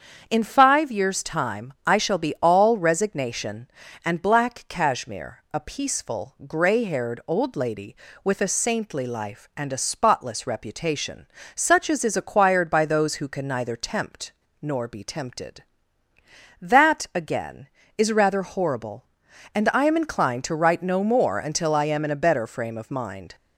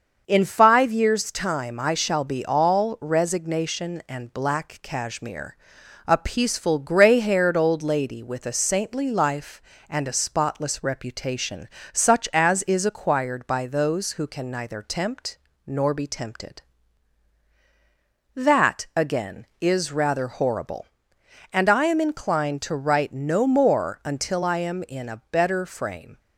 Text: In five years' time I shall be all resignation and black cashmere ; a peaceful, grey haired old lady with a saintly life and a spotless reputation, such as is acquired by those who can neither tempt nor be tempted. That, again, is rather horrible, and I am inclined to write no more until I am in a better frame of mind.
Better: first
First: starts louder than the rest; strong; until 1.2 s; 7.5 dB // pauses between "tempt" and "nor"; slight; at 14.3 s; 0.27 s long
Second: starts louder than the rest; until 1.2 s; 6.5 dB // pauses between "tempt" and "nor"; slight; at 15.3 s; 0.30 s long // stops before "of mind"; at 26.1 s

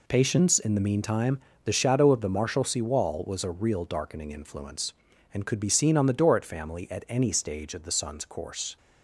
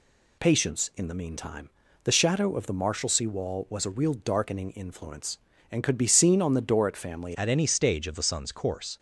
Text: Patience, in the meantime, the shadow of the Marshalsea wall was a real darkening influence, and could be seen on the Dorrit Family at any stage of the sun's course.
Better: first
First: none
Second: changes voice at "at"; from 7.3 s on; 1.6 s long

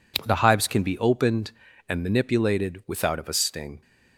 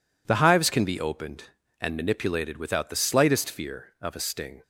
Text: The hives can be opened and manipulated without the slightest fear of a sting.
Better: second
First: skips "the slightest fear"; at 3.1 s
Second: none

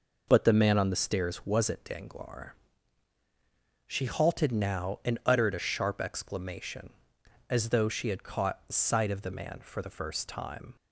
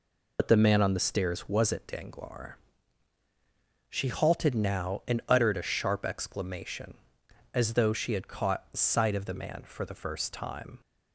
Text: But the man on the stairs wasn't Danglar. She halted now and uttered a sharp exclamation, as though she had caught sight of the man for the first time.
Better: first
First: none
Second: loses the start of "But"; at 0.3 s; 70 ms

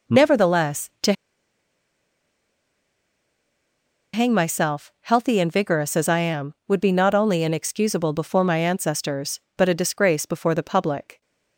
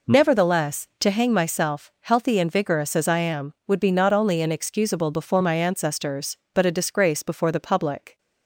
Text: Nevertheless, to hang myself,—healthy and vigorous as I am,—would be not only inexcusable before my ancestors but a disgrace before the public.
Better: second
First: pauses between "to" and "hang"; strong; at 1.1 s; 3.0 s long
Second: none

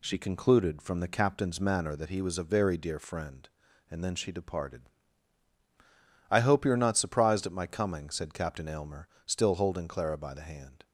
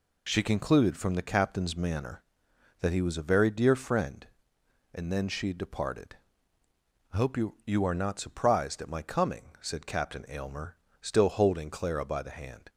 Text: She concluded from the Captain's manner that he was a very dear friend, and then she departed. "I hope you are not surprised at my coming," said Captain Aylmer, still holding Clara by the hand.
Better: first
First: none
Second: says "you" twice; at 7.6 s

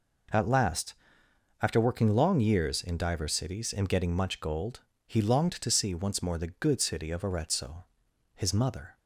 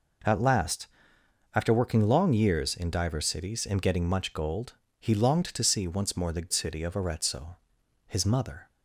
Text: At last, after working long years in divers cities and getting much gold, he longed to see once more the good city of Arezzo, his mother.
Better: first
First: none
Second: skips "good"; at 6.5 s

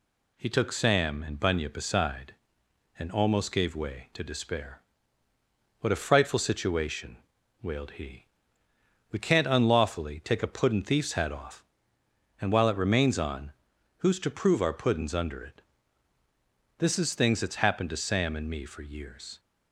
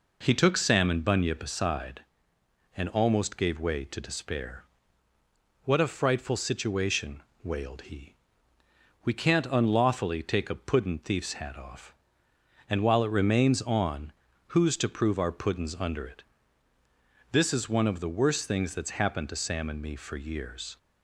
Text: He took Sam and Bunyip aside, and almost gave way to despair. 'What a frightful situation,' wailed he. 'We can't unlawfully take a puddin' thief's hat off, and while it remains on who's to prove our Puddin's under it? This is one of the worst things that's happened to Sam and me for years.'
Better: second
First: pauses between "on" and "who's"; noticeable; at 13.5 s; 0.46 s long // skips "one of the worst"; at 17.1 s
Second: pauses between "on" and "who's"; at 14.1 s; 0.38 s long

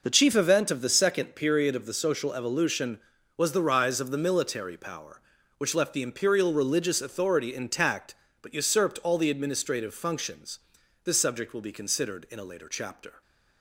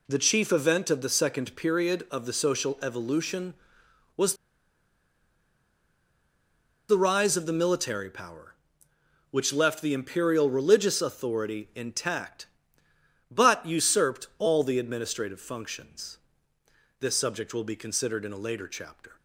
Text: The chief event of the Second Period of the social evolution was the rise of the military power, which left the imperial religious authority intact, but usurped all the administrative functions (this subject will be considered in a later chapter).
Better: first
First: none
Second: pauses between "was" and "the"; strong; at 4.3 s; 2.5 s long

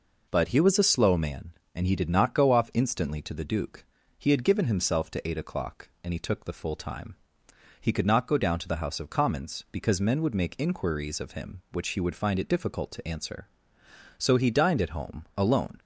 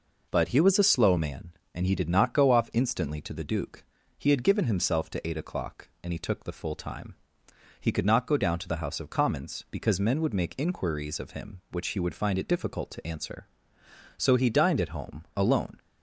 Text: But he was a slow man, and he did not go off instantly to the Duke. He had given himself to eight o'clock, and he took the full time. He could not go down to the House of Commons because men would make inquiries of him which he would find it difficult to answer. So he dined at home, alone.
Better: neither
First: none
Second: none

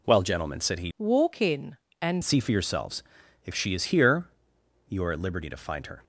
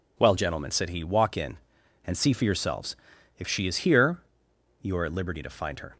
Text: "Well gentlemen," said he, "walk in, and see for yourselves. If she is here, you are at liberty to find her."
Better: second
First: changes voice from "walk" to "and"; from 0.9 to 2.2 s; 1.3 s long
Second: none

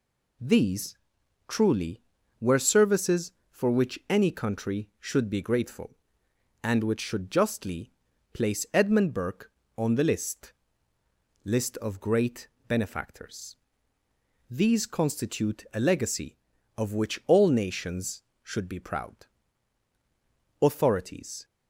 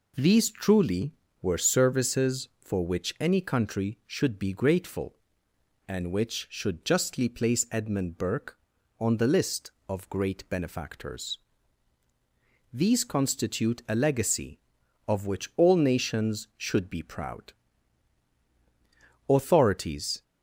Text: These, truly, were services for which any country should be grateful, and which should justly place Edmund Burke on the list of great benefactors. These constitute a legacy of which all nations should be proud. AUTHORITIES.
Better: second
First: pauses between "justly" and "place"; at 7.9 s; 0.42 s long // says "list" twice; at 11.4 s // pauses between "great" and "benefactors"; slight; at 12.4 s; 0.22 s long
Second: none

